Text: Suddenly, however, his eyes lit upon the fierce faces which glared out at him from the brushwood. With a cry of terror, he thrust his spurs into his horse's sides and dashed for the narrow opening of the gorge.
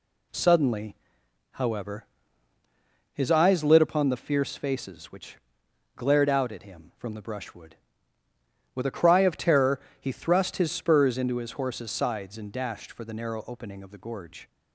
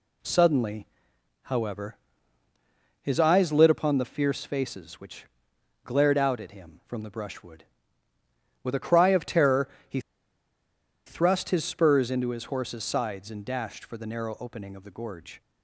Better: first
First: pauses between "which" and "glared"; noticeable; at 5.3 s; 0.60 s long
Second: pauses between "which" and "glared"; noticeable; at 5.2 s; 0.60 s long // pauses between "he" and "thrust"; at 10.0 s; 1.0 s long

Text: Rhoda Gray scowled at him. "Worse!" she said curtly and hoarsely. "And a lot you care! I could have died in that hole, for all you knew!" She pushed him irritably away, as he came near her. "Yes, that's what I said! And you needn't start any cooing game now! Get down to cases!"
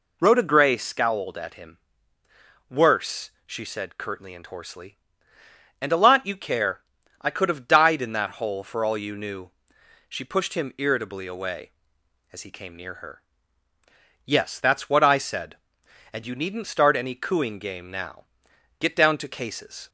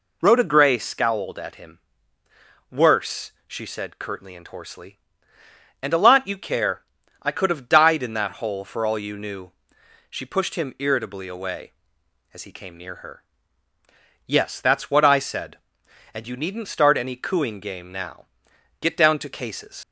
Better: first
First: none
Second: leaves "cases" unfinished; at 19.8 s; 65 ms

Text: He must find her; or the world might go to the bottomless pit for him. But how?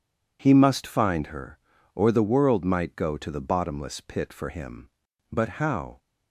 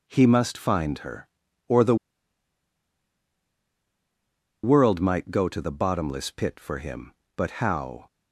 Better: first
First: none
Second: pauses between "the" and "world"; strong; at 1.9 s; 2.6 s long

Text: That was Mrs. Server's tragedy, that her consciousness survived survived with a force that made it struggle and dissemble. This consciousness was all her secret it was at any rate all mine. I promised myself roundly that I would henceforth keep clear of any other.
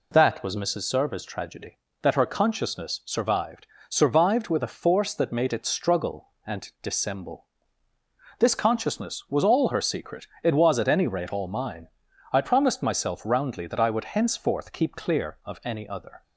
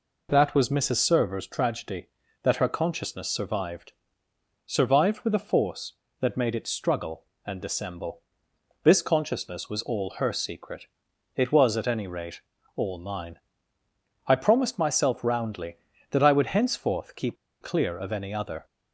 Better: first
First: pauses between "survived" and "survived"; slight; at 3.6 s; 0.22 s long // pauses between "secret" and "it"; slight; at 10.2 s; 0.16 s long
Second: pauses between "survived" and "survived"; noticeable; at 3.9 s; 0.72 s long // pauses between "secret" and "it"; noticeable; at 10.8 s; 0.48 s long // pauses between "rate" and "all"; slight; at 12.4 s; 0.34 s long // pauses between "keep" and "clear"; slight; at 17.3 s; 0.24 s long

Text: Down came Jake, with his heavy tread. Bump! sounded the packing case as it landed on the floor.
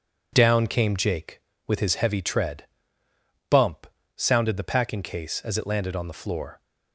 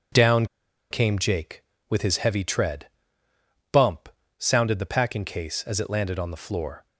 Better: first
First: none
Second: pauses between "Down" and "came"; at 0.4 s; 0.45 s long

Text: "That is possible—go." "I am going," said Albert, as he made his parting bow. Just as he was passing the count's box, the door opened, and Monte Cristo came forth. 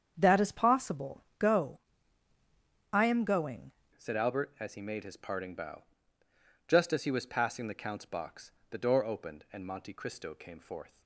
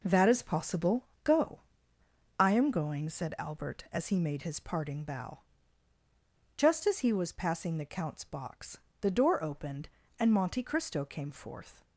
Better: second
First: starts louder than the rest; strong; until 1.1 s; 8 dB // changes voice at "said"; from 3.9 s on; 7.1 s long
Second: none

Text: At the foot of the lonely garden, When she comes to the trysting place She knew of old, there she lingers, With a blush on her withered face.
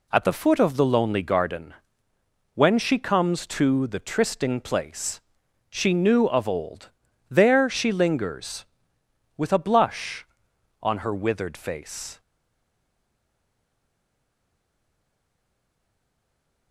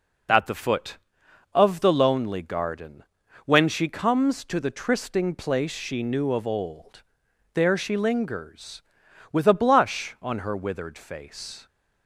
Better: second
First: pauses between "place" and "She"; noticeable; at 5.1 s; 0.50 s long // stays silent after the last word; strong; from 12.1 s on; 4.6 s long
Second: none

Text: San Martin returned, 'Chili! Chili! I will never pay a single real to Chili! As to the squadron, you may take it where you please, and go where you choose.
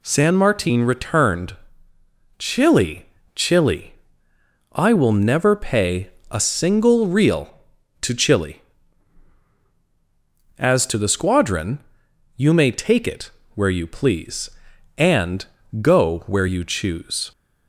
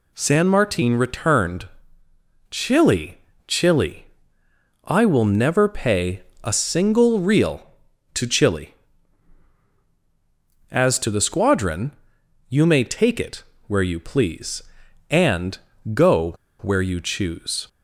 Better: first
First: pauses between "pay" and "a"; slight; at 6.0 s; 0.22 s long // pauses between "it" and "where"; slight; at 13.3 s; 0.24 s long // pauses between "and" and "go"; slight; at 15.4 s; 0.36 s long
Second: pauses between "pay" and "a"; slight; at 6.2 s; 0.22 s long // pauses between "it" and "where"; slight; at 13.4 s; 0.24 s long // pauses between "and" and "go"; slight; at 15.5 s; 0.36 s long // pauses between "go" and "where"; slight; at 16.3 s; 0.26 s long

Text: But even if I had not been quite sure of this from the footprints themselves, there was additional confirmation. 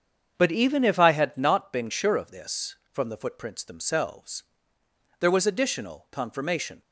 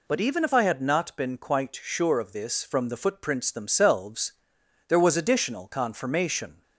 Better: second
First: starts louder than the rest; strong; until 1.3 s; 7.5 dB // skips "quite"; at 1.9 s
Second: none

